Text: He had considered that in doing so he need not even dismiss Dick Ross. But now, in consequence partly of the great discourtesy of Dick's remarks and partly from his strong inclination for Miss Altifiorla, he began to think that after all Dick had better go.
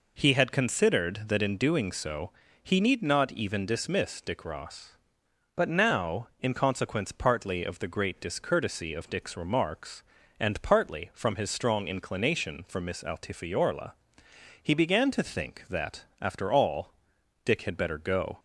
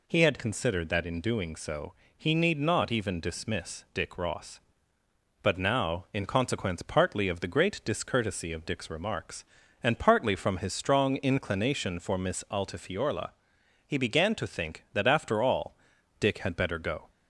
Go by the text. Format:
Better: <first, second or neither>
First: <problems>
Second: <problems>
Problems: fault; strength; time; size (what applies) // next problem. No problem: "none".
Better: neither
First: pauses between "so" and "he"; slight; at 2.3 s; 0.32 s long // pauses between "all" and "Dick"; noticeable; at 16.9 s; 0.52 s long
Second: pauses between "so" and "he"; slight; at 1.9 s; 0.24 s long // pauses between "all" and "Dick"; at 15.7 s; 0.44 s long